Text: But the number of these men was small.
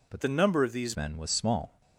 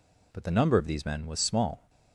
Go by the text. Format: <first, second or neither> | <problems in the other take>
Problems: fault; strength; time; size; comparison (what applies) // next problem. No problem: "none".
second | changes voice from "the" to "these"; from 0.2 to 0.9 s; 0.7 s long